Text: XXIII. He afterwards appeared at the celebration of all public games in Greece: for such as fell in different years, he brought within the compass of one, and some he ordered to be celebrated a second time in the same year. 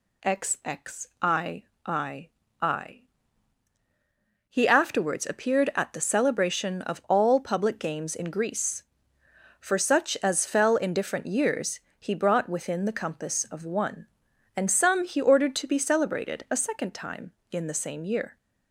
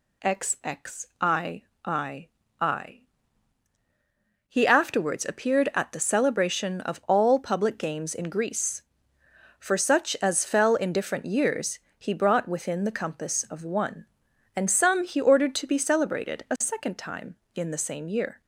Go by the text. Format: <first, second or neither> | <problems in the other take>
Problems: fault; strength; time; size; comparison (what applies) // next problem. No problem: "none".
neither | none